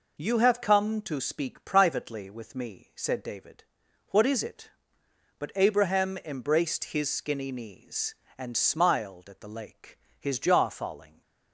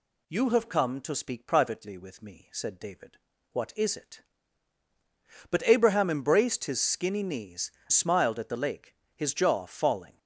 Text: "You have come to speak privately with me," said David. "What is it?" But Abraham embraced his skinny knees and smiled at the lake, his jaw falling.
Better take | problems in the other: first | skips "and"; at 7.8 s

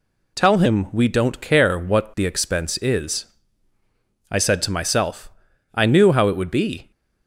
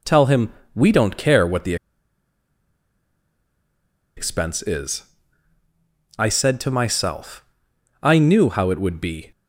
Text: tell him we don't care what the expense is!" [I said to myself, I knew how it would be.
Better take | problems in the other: first | pauses between "him" and "we"; slight; at 0.5 s; 0.24 s long // pauses between "the" and "expense"; strong; at 1.7 s; 2.4 s long

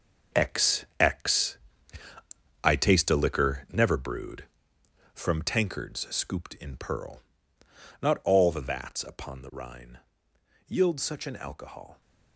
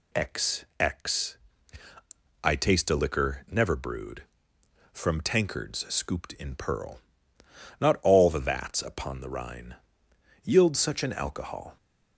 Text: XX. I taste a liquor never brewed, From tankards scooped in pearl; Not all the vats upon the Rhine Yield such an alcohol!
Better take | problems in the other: second | gets quieter; strong; throughout; 9.5 dB // pauses between "Rhine" and "Yield"; noticeable; at 10.0 s; 0.66 s long; noticeable in the second

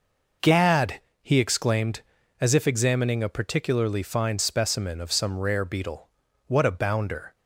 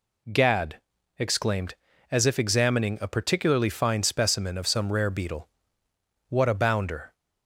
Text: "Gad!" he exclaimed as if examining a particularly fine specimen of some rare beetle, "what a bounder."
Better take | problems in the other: first | skips "he"; at 0.9 s

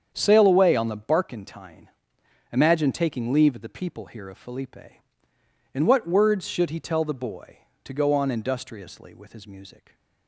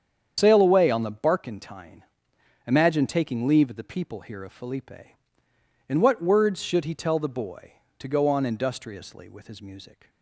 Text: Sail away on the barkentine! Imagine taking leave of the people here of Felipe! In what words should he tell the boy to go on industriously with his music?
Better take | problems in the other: first | loses the start of "Sail"; at 0.3 s; 90 ms // starts louder than the rest; strong; until 1.3 s; 8 dB; strong in the first

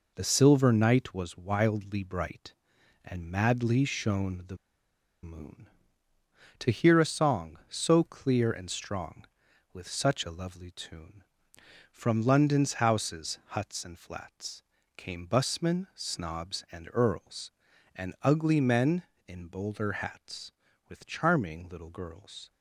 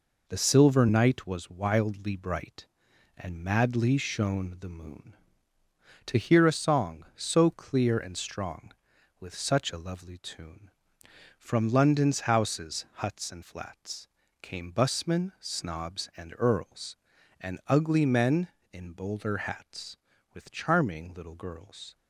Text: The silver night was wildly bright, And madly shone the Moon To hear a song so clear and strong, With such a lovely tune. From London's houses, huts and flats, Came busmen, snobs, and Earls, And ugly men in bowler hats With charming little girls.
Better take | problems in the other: second | pauses between "the" and "Moon"; noticeable; at 4.5 s; 0.66 s long

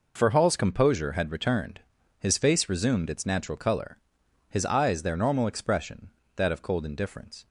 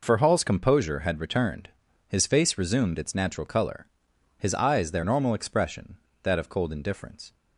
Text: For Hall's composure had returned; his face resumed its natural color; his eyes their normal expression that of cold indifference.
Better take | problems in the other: neither | none

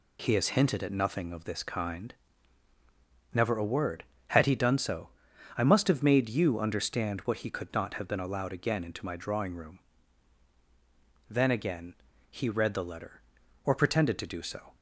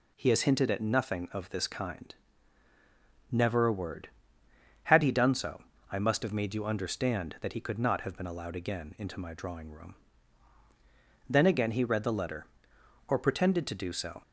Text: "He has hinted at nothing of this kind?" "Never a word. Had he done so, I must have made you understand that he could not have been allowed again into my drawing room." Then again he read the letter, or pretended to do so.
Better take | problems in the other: second | says "what" for "that"; at 7.2 s // pauses between "again" and "he"; slight; at 11.9 s; 0.34 s long

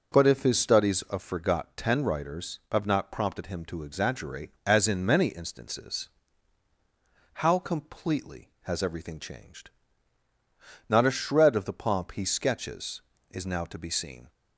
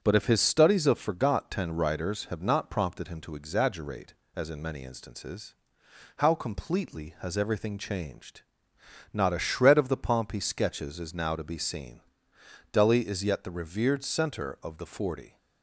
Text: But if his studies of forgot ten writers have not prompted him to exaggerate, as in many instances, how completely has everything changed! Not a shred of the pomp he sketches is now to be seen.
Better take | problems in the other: first | starts louder than the rest; noticeable; until 1.0 s; 6 dB // goes on to say "Delhi is yet the revered center of the forty"; strong; from 12.7 s on; 2.6 s long

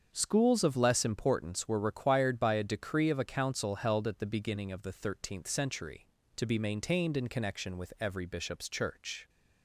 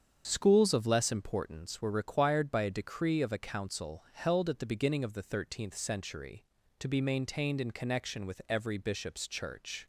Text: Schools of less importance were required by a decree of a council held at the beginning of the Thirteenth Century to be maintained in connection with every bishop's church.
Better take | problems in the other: neither | starts louder than the rest; strong; the same in both

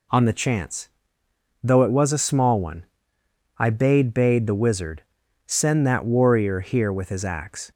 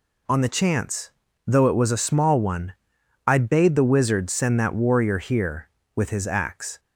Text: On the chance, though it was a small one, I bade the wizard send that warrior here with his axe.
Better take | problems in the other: second | says "bade" twice; at 4.1 s // pauses between "wizard" and "send"; at 5.0 s; 0.42 s long

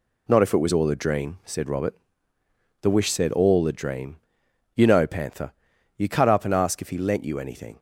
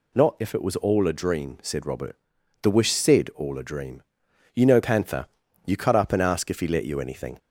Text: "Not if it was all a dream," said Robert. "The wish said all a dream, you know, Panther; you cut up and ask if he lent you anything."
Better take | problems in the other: first | says "let" for "lent"; at 6.6 s

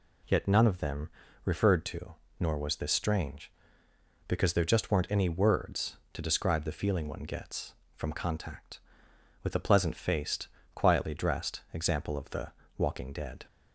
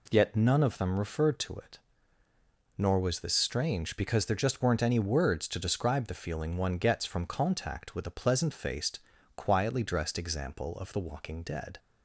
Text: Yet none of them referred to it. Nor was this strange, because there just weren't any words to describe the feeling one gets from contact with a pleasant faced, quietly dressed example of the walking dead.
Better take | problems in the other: second | pauses between "them" and "referred"; slight; at 1.0 s; 0.36 s long // skips "it"; at 2.2 s // pauses between "the" and "walking"; slight; at 12.5 s; 0.26 s long

